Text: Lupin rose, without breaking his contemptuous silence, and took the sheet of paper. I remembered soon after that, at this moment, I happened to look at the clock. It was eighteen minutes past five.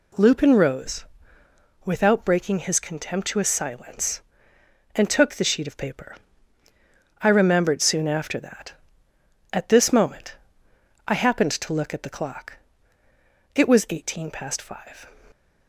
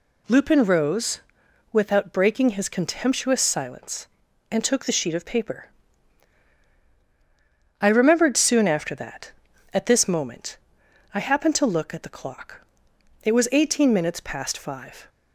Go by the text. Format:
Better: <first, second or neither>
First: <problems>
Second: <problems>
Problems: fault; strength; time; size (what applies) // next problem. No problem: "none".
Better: second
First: skips "minutes"; at 14.2 s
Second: none